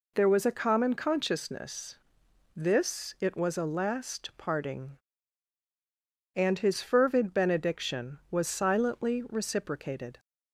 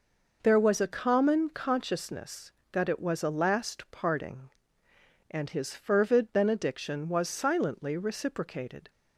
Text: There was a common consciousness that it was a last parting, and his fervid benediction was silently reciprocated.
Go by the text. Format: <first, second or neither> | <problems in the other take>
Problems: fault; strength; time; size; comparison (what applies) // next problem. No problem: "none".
second | says "this" for "that"; at 2.5 s